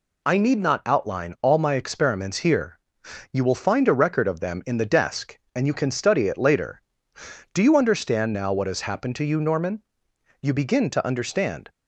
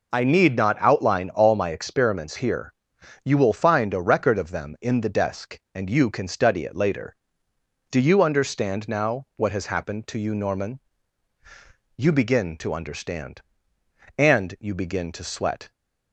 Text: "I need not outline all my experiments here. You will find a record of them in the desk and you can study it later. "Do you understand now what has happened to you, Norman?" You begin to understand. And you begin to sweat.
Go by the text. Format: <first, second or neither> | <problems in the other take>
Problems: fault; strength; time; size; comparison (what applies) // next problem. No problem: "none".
second | stops before "And you begin to sweat"; at 11.6 s